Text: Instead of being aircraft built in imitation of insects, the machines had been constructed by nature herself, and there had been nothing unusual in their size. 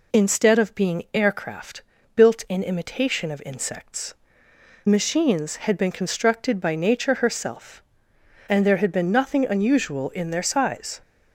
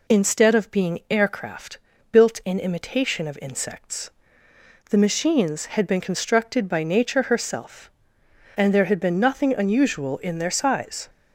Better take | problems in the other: second | pauses between "aircraft" and "built"; slight; at 1.8 s; 0.34 s long; slight in the second // skips "the"; at 4.5 s

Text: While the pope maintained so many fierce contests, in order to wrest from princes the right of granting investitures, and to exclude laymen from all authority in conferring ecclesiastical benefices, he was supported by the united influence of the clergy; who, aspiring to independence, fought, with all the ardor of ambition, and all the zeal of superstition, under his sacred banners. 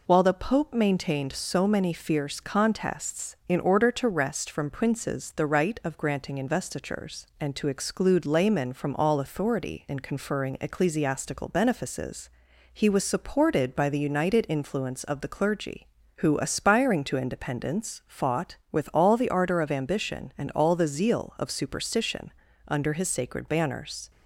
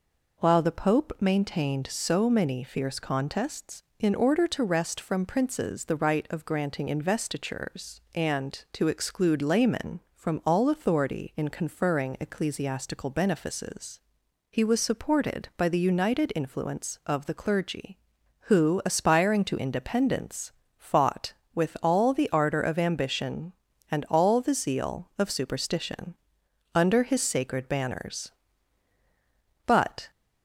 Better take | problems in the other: first | goes on to say "But"; slight; from 29.6 s on; 0.44 s long

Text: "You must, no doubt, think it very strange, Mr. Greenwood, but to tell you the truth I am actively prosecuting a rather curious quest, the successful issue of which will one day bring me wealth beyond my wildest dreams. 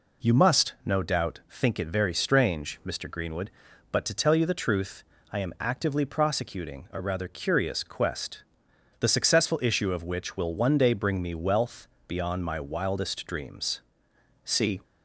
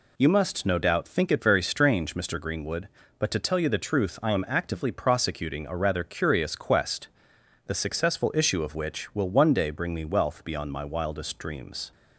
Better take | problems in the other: second | pauses between "truth" and "I"; slight; at 5.0 s; 0.30 s long // pauses between "wealth" and "beyond"; slight; at 11.8 s; 0.20 s long // goes on to say "See"; slight; from 14.4 s on; 0.36 s long

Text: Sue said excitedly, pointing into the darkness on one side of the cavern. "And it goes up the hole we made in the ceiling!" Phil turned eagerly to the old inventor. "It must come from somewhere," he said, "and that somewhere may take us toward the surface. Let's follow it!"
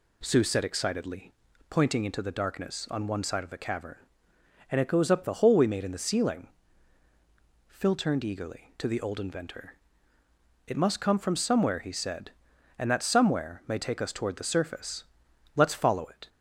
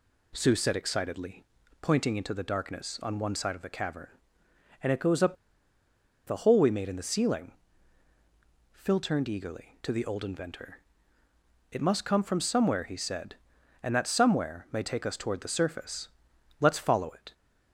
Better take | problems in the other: first | pauses between "up" and "the"; noticeable; at 5.3 s; 0.91 s long

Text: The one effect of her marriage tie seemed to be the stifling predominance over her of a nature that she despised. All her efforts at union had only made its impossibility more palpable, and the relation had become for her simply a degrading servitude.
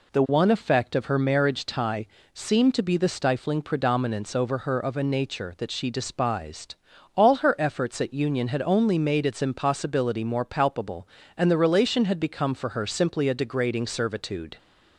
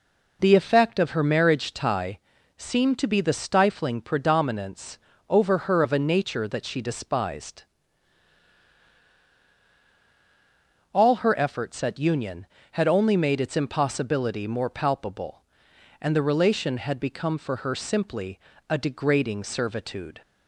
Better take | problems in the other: first | skips "one"; at 0.5 s // pauses between "tie" and "seemed"; at 2.1 s; 0.38 s long; slight in the first // pauses between "predominance" and "over"; slight; at 4.9 s; 0.32 s long // pauses between "simply" and "a"; slight; at 18.3 s; 0.30 s long

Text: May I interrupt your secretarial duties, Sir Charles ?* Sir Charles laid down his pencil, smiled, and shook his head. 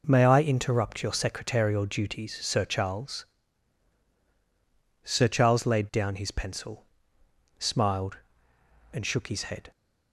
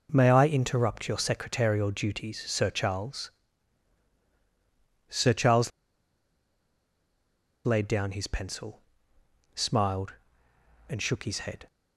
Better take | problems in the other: first | pauses between "Charles" and "laid"; strong; at 5.7 s; 1.9 s long

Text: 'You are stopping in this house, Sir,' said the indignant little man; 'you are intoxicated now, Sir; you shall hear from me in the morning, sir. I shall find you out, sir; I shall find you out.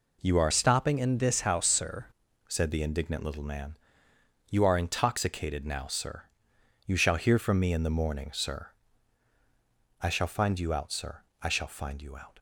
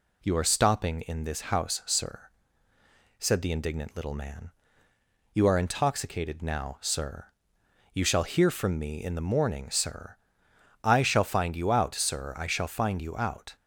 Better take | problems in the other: second | changes voice from "stopping" to "Sir"; from 0.5 to 2.0 s; 1.5 s long

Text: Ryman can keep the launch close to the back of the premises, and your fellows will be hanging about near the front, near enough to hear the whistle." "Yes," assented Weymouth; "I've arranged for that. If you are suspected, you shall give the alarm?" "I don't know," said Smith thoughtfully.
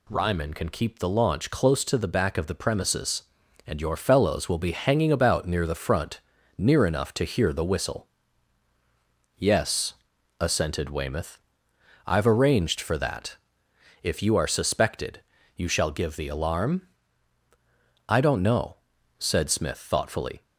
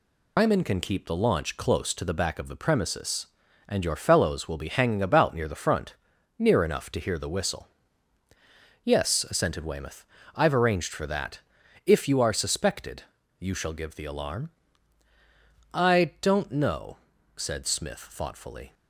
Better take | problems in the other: first | loses the start of "Ryman"; at 0.3 s; 135 ms

